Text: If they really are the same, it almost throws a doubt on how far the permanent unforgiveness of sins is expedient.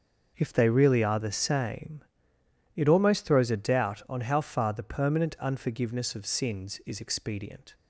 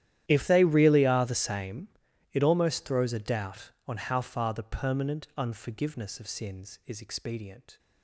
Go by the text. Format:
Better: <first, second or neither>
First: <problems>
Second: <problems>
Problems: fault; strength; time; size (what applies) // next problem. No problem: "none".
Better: first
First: starts louder than the rest; until 1.3 s; 6 dB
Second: gets quieter; strong; throughout; 23 dB // starts louder than the rest; strong; until 1.2 s; 12 dB